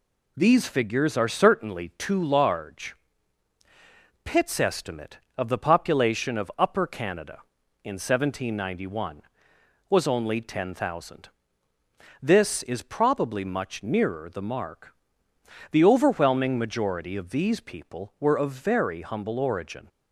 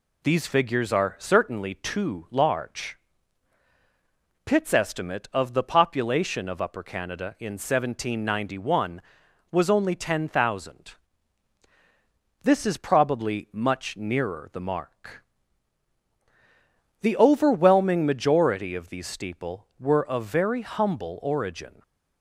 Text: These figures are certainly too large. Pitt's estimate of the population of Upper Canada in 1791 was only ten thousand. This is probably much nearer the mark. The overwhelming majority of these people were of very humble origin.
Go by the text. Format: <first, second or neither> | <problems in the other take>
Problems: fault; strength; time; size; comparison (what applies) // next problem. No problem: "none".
first | says "steeple" for "people"; at 19.0 s // stays silent after the last word; slight; from 21.6 s on; 0.6 s long